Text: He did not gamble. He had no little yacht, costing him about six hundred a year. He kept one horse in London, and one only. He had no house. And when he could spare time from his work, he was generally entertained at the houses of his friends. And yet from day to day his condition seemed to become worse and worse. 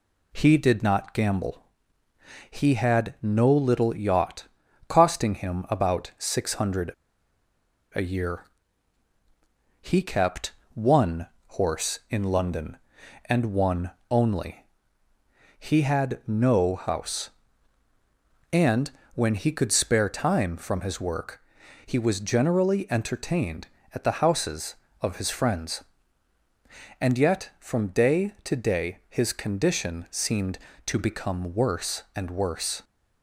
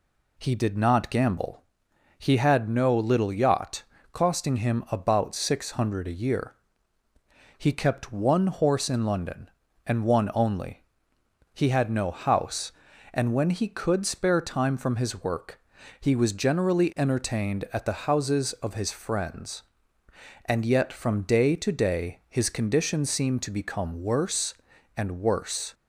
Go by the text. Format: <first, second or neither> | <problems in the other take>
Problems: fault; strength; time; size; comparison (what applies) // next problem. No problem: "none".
second | pauses between "hundred" and "a"; at 6.9 s; 1.0 s long // pauses between "kept" and "one"; slight; at 10.5 s; 0.22 s long // pauses between "one" and "horse"; slight; at 11.2 s; 0.30 s long // pauses between "one" and "only"; slight; at 13.9 s; 0.18 s long // pauses between "And" and "when"; slight; at 18.8 s; 0.24 s long